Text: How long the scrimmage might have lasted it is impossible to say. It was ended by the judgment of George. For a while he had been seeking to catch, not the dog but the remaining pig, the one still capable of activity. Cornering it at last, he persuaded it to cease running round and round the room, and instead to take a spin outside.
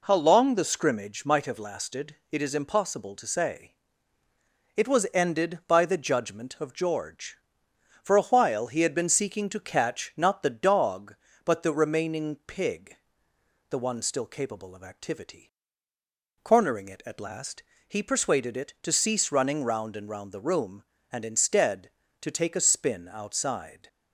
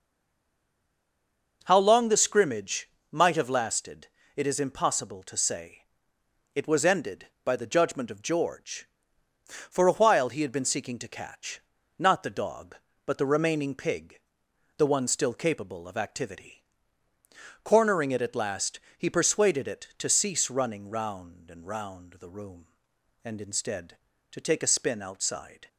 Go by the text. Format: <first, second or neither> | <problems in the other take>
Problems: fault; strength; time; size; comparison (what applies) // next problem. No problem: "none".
first | stays silent before the first word; noticeable; until 1.6 s; 1.6 s long // pauses between "scrimmage" and "might"; slight; at 2.8 s; 0.22 s long // pauses between "lasted" and "it"; slight; at 4.0 s; 0.28 s long